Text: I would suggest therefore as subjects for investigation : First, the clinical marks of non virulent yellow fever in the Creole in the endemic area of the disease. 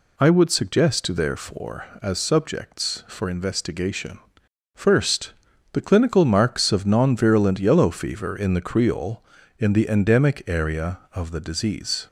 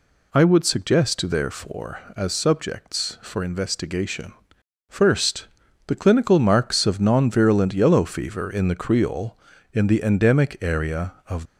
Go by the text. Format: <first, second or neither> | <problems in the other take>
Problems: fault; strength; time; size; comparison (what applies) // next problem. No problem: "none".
first | stops before "the disease"; at 11.4 s